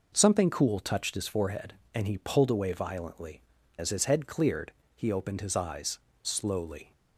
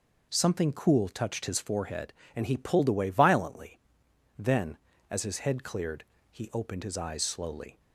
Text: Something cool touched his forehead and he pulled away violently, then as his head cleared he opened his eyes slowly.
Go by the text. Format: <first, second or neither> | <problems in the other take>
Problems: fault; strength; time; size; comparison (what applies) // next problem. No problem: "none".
second | skips "then"; at 3.5 s // pauses between "cleared" and "he"; slight; at 4.7 s; 0.24 s long; slight in the second // pauses between "eyes" and "slowly"; slight; at 5.9 s; 0.24 s long